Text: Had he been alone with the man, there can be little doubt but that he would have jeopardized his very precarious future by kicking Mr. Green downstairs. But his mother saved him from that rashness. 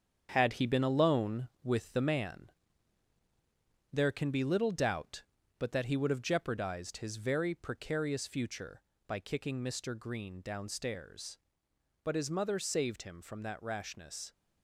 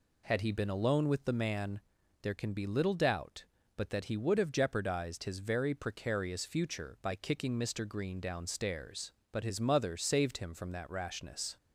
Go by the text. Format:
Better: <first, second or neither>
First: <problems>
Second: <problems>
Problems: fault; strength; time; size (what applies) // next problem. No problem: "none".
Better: second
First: gets quieter; throughout; 6.5 dB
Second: none